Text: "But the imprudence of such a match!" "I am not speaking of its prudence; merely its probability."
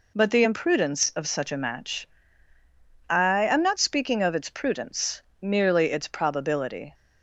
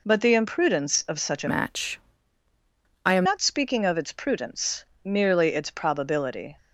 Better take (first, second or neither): first